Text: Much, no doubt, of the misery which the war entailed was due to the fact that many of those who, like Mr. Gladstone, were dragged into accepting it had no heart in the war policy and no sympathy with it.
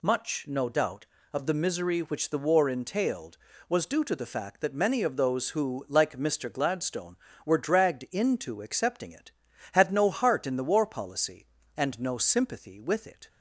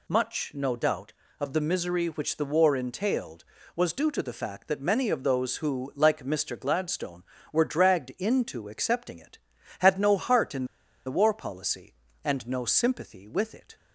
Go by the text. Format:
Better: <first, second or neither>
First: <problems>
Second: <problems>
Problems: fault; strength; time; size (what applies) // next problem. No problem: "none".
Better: first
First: none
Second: pauses between "in" and "the"; at 10.6 s; 0.41 s long